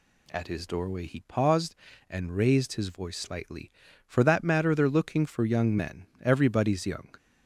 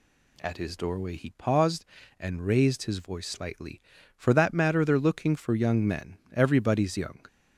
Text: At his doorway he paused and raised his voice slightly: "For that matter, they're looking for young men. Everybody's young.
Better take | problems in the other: neither | none

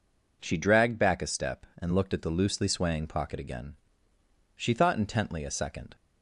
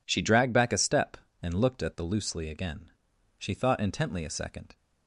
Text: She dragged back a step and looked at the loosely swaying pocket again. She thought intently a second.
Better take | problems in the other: first | skips "swaying pocket"; at 2.4 s

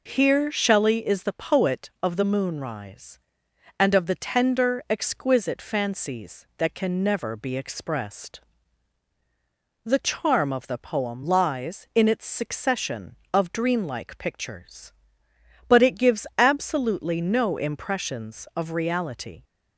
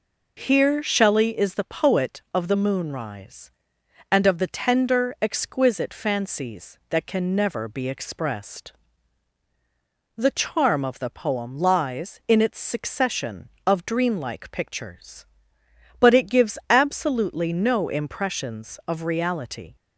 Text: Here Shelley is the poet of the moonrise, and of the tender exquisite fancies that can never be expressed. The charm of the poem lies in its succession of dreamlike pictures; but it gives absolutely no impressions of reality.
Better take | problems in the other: neither | none

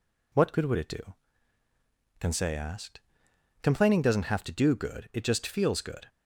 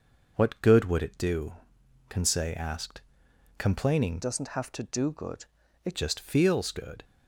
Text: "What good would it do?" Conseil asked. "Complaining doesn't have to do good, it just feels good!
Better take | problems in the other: first | changes voice from "doesn't" to "it"; from 4.2 to 5.9 s; 1.7 s long

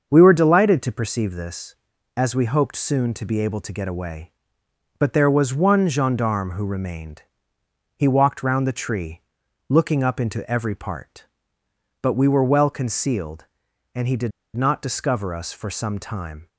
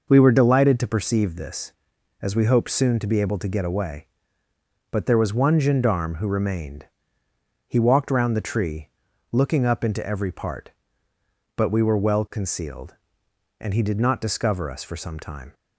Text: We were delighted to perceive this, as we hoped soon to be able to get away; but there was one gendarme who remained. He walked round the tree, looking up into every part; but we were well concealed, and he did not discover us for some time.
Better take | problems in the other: second | starts louder than the rest; until 1.1 s; 6.5 dB // pauses between "did" and "not"; slight; at 14.3 s; 0.24 s long

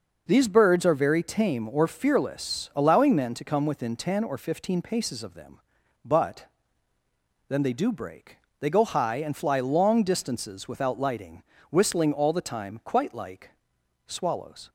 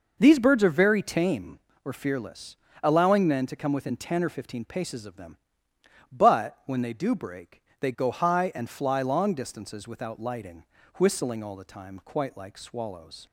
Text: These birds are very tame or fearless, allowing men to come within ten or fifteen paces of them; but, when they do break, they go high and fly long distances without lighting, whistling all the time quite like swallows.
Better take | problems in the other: second | says "then" for "when"; at 7.4 s // pauses between "like" and "swallows"; noticeable; at 13.4 s; 0.56 s long

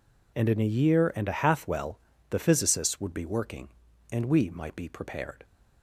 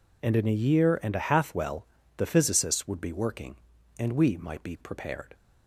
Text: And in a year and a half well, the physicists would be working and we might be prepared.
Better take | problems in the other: neither | none

